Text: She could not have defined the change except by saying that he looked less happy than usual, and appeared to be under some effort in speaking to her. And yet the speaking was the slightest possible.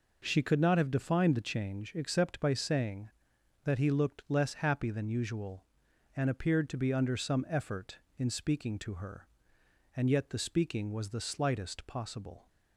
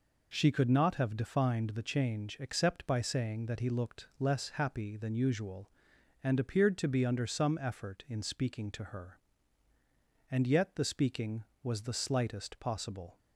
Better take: neither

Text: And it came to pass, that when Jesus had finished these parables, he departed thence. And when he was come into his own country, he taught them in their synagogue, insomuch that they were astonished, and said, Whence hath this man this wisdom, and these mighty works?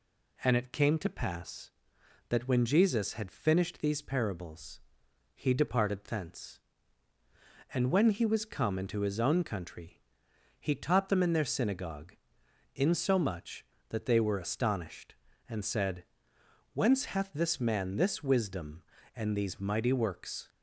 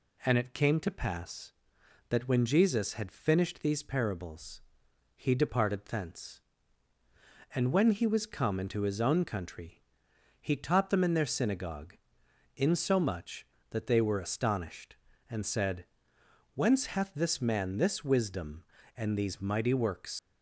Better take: first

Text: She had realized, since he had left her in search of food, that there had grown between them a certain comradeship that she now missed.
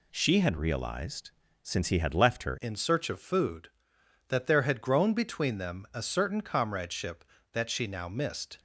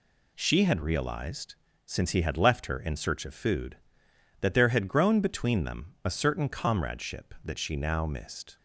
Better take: second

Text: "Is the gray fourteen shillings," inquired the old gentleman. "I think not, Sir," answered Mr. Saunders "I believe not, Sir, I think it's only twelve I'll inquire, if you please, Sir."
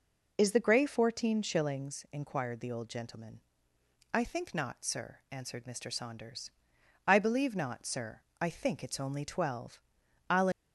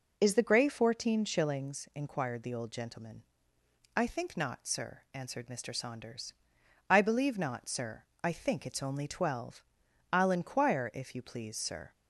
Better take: second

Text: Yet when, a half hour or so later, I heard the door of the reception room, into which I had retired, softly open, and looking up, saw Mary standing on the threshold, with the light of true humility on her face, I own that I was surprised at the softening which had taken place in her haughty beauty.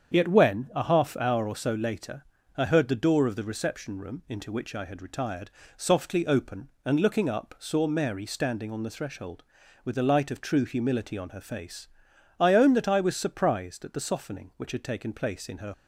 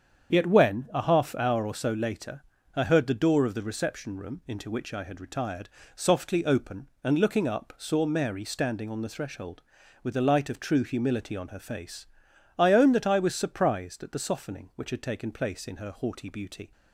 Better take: second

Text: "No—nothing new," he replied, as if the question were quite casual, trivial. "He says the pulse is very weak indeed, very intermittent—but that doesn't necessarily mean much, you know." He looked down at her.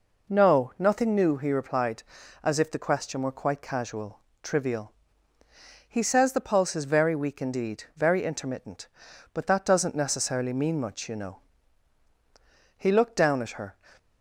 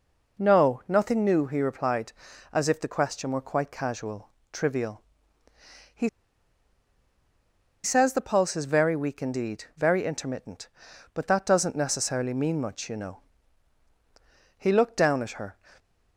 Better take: first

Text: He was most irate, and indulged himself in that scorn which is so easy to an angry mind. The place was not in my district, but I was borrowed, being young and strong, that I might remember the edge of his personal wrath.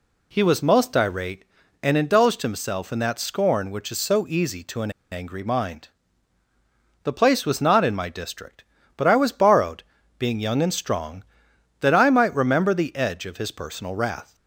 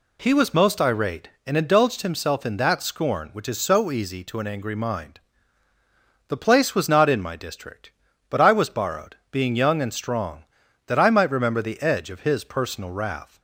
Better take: second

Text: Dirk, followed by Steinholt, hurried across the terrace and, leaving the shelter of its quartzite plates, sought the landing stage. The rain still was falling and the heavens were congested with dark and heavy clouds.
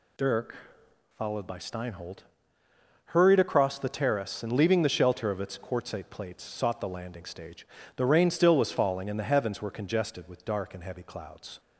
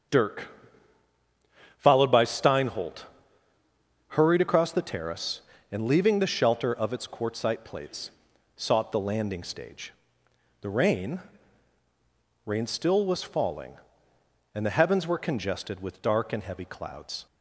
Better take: first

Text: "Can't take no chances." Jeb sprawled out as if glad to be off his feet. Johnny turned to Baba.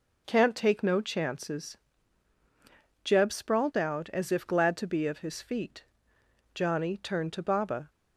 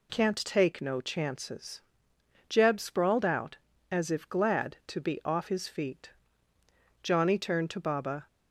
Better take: second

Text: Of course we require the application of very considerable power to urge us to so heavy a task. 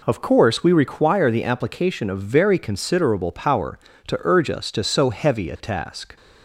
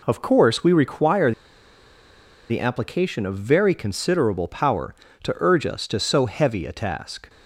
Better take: first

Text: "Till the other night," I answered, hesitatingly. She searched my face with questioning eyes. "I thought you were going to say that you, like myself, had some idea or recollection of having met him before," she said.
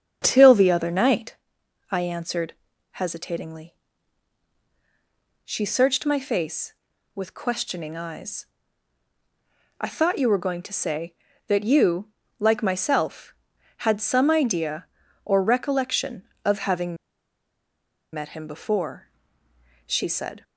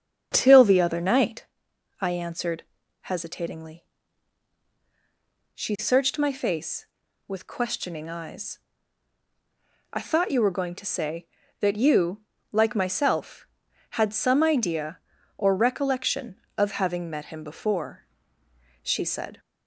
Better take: second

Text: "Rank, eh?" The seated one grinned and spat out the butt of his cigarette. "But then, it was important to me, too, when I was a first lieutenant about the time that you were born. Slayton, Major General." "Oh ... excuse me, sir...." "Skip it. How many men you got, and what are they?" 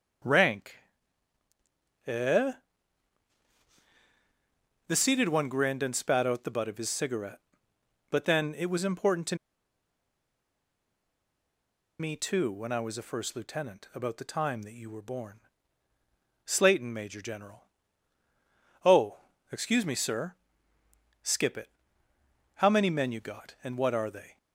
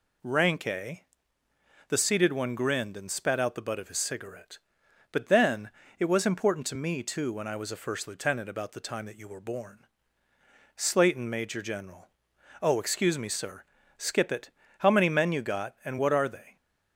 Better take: second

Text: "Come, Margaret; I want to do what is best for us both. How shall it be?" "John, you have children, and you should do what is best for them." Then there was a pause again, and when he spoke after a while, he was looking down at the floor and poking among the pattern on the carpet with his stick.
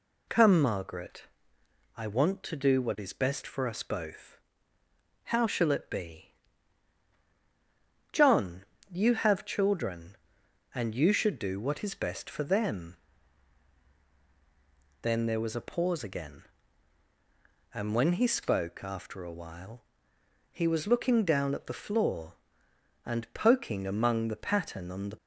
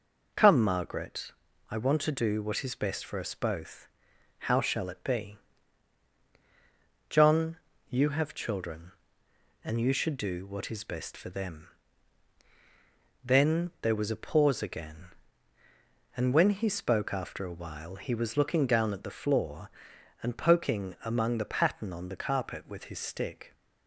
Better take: second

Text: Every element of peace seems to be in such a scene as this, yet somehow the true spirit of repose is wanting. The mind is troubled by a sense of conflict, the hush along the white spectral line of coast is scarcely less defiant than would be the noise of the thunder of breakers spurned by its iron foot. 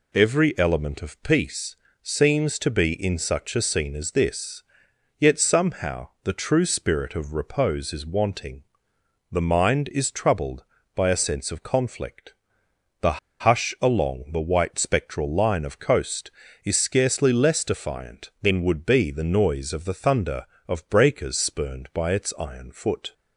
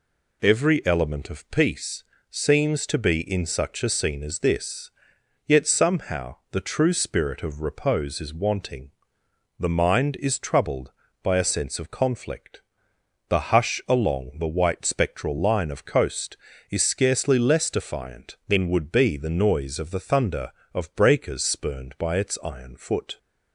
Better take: second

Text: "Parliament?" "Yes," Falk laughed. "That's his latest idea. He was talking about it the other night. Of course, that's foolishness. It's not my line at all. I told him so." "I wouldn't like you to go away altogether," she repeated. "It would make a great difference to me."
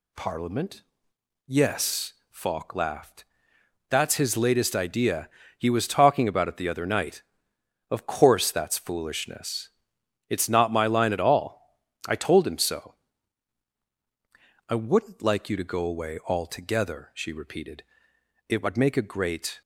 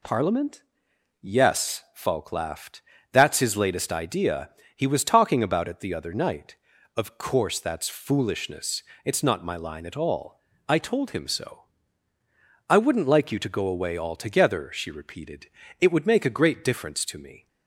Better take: second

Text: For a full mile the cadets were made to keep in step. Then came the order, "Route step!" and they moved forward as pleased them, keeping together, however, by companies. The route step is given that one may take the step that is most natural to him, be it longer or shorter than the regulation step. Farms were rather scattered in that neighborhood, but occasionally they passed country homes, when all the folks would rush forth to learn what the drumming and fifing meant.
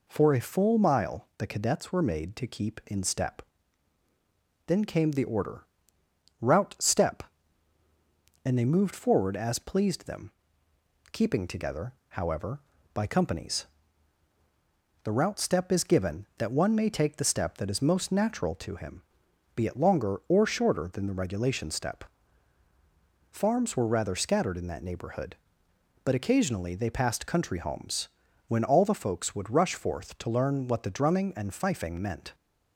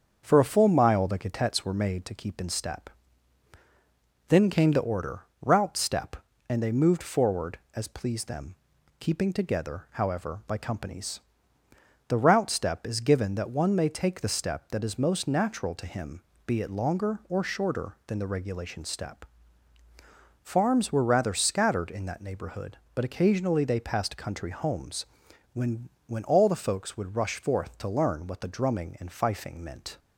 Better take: first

